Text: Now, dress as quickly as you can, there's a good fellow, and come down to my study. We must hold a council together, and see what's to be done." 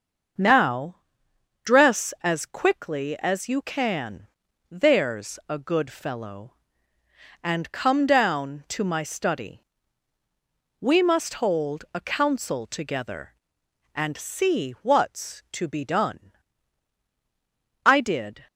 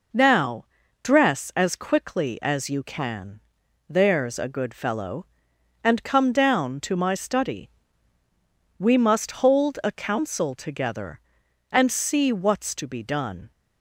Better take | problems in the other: second | starts louder than the rest; until 2.0 s; 6.5 dB // goes on to say "I did"; noticeable; from 17.8 s on; 0.64 s long

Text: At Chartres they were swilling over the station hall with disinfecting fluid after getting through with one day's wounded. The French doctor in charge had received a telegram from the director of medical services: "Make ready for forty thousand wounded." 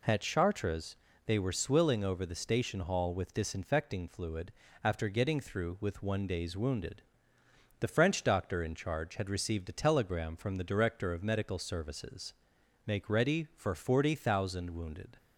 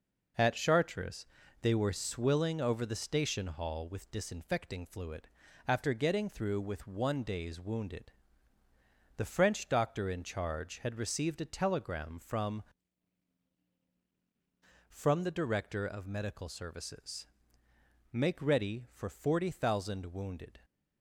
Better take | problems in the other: first | pauses between "Chartres" and "they"; slight; at 1.2 s; 0.34 s long; slight in the first // pauses between "fluid" and "after"; at 5.2 s; 0.38 s long; slight in the first // says "from" twice; at 14.8 s

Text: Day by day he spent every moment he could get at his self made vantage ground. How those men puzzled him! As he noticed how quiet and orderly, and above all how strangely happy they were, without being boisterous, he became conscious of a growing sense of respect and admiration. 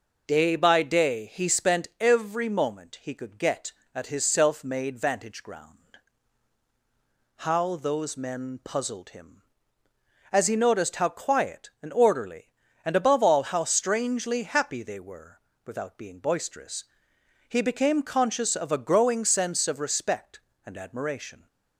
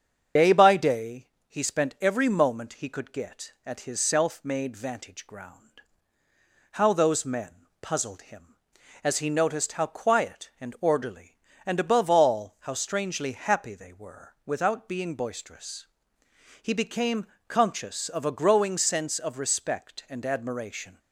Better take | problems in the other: first | loses the start of "Day"; at 0.3 s; 70 ms // starts louder than the rest; strong; until 1.5 s; 7.5 dB // pauses between "day" and "he"; slight; at 1.2 s; 0.18 s long // pauses between "men" and "puzzled"; slight; at 7.5 s; 0.30 s long // pauses between "became" and "conscious"; slight; at 17.2 s; 0.20 s long

